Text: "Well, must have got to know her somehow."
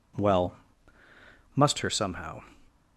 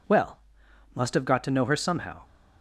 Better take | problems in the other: second | skips "have got to know"; at 1.8 s

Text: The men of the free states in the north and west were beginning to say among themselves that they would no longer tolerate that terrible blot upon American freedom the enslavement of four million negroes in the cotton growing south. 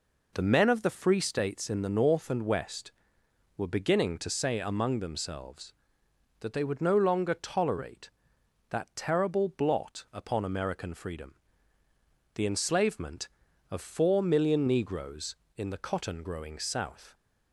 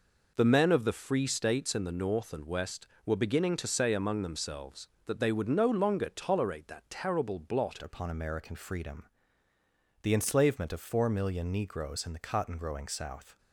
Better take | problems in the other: first | changes voice at "upon"; from 7.8 s on; 5.5 s long // pauses between "freedom" and "the"; noticeable; at 9.0 s; 0.96 s long; also in the first

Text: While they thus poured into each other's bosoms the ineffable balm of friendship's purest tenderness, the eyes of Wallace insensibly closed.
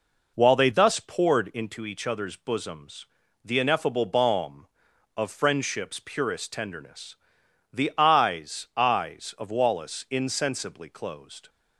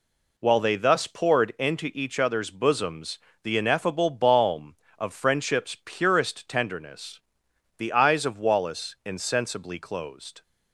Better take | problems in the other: second | pauses between "bosoms" and "the"; at 3.0 s; 0.40 s long; slight in the second // says "eyes" twice; at 8.7 s

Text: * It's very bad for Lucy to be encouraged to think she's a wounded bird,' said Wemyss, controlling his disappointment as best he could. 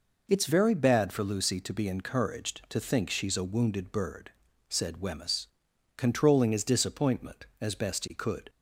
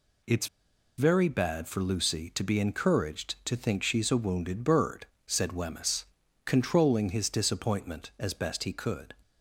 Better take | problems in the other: first | pauses between "It's" and "very"; noticeable; at 0.4 s; 0.51 s long

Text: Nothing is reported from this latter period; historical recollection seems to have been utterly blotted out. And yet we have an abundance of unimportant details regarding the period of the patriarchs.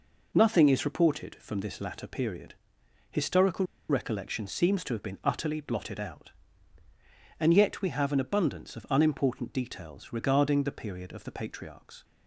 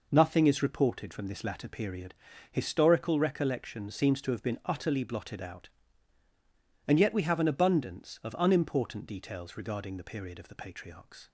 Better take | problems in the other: second | pauses between "historical" and "recollection"; slight; at 3.6 s; 0.23 s long

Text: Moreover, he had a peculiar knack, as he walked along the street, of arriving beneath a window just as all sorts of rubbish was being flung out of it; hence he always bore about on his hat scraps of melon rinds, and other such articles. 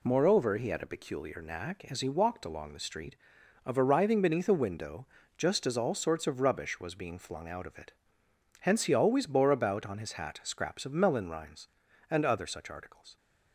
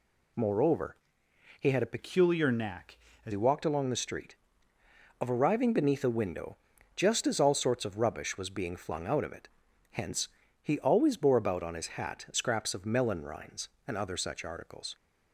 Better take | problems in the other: first | changes voice from "peculiar" to "as"; from 1.9 to 3.3 s; 1.4 s long // pauses between "window" and "just"; at 6.5 s; 0.38 s long; slight in the first // pauses between "hence" and "he"; slight; at 10.2 s; 0.32 s long

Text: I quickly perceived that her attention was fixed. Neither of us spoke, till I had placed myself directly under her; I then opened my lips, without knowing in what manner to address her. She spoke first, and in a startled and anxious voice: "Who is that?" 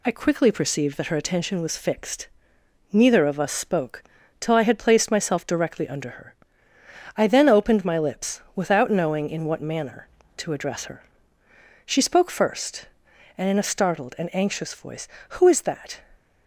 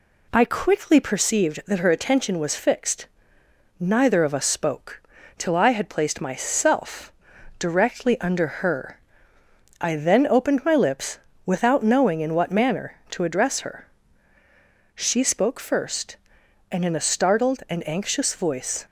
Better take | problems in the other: first | pauses between "myself" and "directly"; noticeable; at 7.1 s; 0.46 s long // pauses between "under" and "her"; slight; at 8.4 s; 0.16 s long // stops before "Who is that"; at 18.8 s

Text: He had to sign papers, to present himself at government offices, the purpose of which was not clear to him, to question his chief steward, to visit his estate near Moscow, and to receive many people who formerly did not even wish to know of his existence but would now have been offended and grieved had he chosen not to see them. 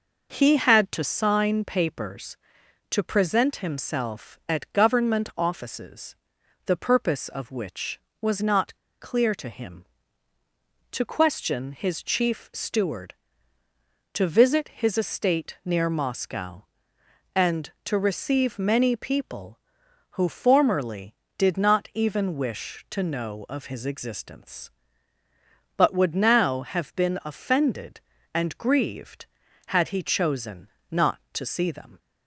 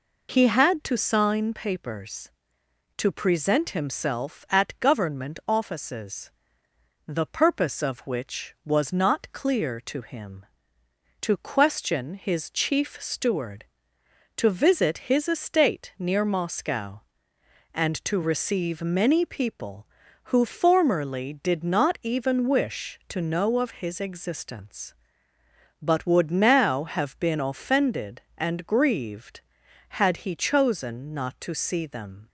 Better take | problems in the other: second | pauses between "not" and "clear"; slight; at 8.7 s; 0.25 s long // pauses between "chosen" and "not"; slight; at 30.6 s; 0.24 s long

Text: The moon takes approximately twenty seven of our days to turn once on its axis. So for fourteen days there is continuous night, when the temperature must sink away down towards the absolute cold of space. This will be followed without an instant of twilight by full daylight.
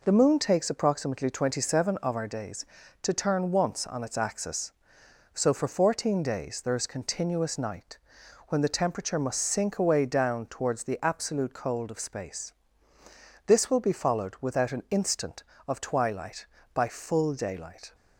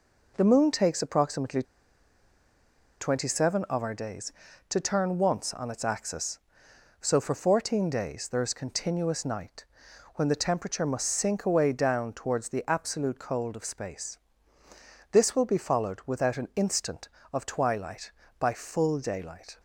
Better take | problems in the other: first | pauses between "approximately" and "twenty"; strong; at 1.6 s; 1.3 s long

